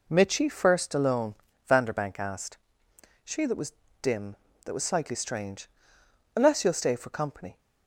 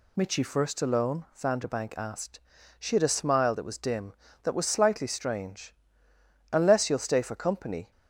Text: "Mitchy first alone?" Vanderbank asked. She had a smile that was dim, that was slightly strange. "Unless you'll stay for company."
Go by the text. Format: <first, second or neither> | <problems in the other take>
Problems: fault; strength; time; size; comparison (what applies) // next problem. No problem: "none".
second | skips "had a smile"; at 3.4 s // pauses between "was" and "dim"; slight; at 3.7 s; 0.28 s long